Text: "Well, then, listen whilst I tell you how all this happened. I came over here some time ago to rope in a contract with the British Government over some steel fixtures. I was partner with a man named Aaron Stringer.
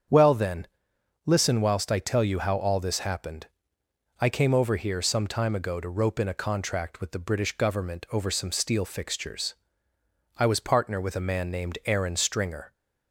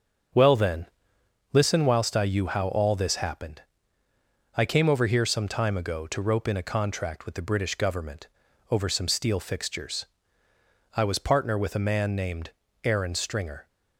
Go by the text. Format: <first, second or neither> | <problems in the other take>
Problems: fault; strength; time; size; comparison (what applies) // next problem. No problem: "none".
first | starts louder than the rest; strong; until 2.0 s; 7.5 dB; strong in the first // skips "tell"; at 2.2 s // pauses between "Government" and "over"; at 8.2 s; 0.42 s long // pauses between "named" and "Aaron"; slight; at 12.5 s; 0.32 s long